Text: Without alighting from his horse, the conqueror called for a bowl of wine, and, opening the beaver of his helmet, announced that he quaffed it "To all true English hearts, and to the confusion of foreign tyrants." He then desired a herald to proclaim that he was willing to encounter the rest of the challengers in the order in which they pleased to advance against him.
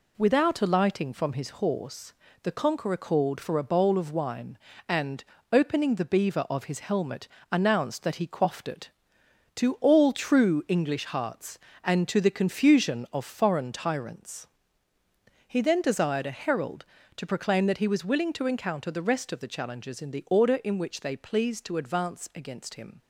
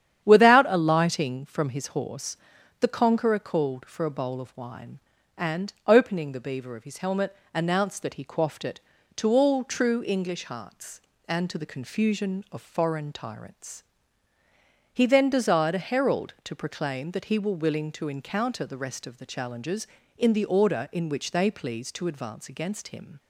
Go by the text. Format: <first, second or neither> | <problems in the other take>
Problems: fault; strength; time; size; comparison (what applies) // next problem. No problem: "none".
first | starts louder than the rest; strong; until 1.2 s; 9.5 dB // says "were" for "was"; at 17.3 s